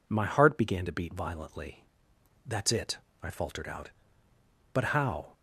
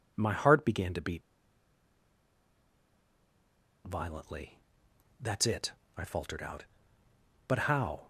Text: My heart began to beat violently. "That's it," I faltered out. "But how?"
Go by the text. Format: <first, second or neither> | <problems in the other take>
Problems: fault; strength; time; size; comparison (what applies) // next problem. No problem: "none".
first | pauses between "beat" and "violently"; strong; at 1.2 s; 2.6 s long